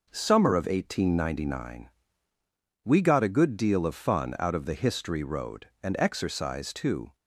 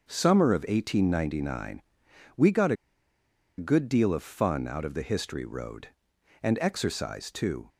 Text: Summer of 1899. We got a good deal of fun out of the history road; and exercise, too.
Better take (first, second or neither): first